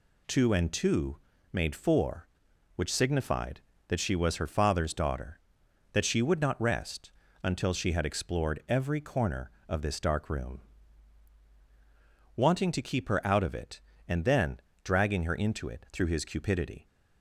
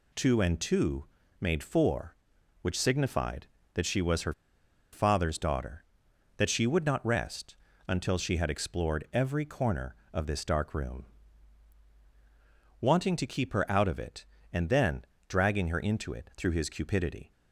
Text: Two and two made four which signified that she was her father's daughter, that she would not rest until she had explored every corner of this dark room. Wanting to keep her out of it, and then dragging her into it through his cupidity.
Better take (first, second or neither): first